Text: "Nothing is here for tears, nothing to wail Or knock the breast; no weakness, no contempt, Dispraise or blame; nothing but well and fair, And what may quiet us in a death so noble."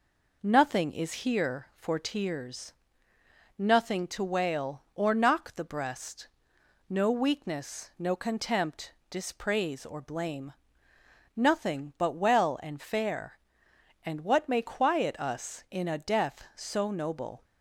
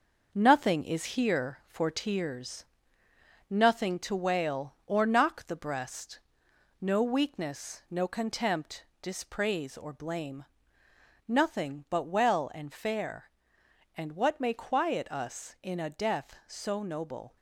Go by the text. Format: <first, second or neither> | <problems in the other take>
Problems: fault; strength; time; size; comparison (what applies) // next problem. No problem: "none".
first | gets quieter; noticeable; throughout; 5 dB